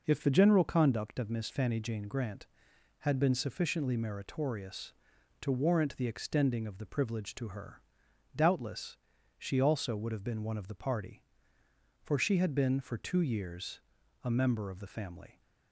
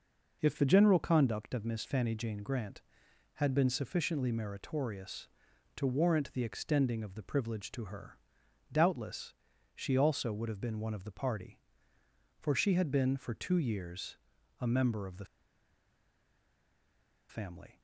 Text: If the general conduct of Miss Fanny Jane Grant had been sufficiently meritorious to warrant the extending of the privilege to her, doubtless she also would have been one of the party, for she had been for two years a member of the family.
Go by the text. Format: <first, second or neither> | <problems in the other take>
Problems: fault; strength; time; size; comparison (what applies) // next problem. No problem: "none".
first | pauses between "doubtless" and "she"; at 9.3 s; 0.40 s long; also in the first // pauses between "years" and "a"; at 14.1 s; 0.44 s long; also in the first // pauses between "the" and "family"; strong; at 15.2 s; 2.0 s long